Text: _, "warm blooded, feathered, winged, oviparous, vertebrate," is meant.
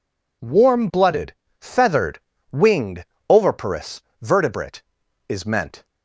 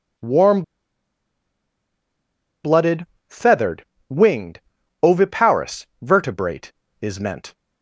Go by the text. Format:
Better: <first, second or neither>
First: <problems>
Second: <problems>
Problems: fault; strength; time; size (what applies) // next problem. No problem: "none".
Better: first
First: none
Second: pauses between "warm" and "blooded"; strong; at 0.6 s; 2.0 s long